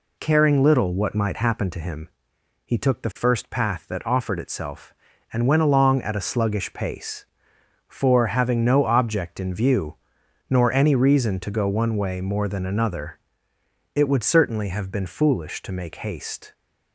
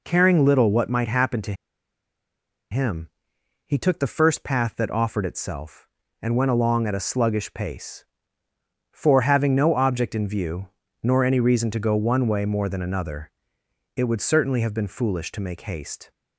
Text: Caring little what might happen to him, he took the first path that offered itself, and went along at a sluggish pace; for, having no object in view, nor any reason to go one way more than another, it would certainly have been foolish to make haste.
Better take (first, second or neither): first